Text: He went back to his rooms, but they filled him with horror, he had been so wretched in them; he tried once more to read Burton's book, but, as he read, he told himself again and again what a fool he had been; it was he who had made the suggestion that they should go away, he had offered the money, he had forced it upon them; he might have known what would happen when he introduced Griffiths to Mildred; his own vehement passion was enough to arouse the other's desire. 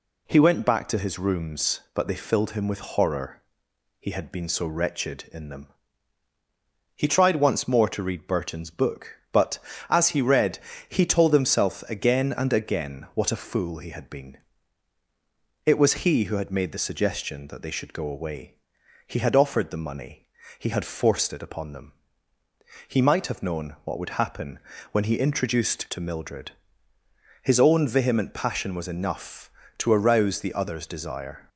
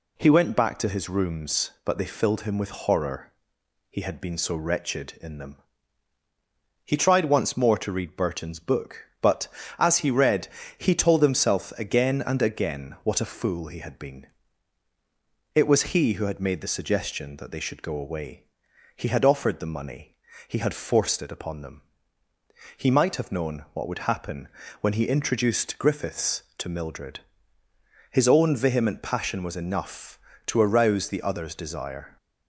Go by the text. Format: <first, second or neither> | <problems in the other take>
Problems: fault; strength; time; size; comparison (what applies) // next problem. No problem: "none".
second | pauses between "happen" and "when"; slight; at 24.5 s; 0.34 s long; slight in the second // skips "Griffiths"; at 25.8 s